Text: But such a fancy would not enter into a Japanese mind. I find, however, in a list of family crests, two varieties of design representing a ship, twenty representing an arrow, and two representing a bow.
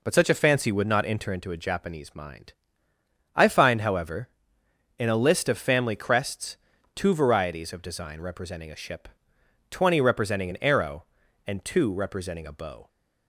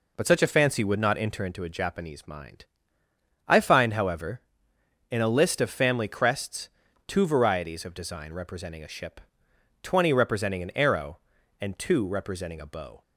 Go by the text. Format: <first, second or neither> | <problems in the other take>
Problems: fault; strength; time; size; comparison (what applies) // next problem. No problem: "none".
neither | none